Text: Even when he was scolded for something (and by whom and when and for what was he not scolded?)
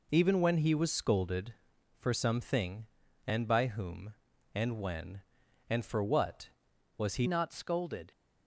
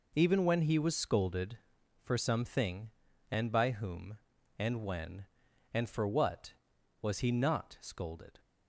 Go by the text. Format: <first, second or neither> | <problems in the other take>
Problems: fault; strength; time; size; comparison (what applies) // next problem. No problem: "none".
second | changes voice at "not"; from 7.2 s on; 0.9 s long